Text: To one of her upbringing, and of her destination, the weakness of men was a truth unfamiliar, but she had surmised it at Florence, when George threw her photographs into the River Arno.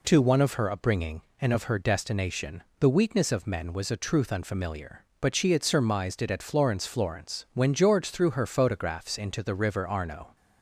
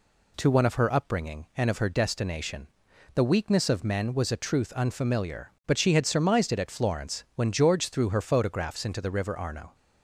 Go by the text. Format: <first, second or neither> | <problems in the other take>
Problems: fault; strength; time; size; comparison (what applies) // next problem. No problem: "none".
second | says "Florence" twice; at 6.8 s